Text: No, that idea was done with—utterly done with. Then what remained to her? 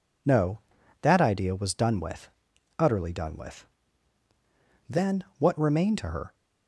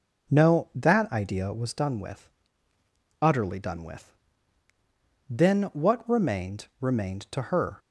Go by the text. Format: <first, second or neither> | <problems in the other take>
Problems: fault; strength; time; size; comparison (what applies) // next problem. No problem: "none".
first | says "remained" twice; at 6.8 s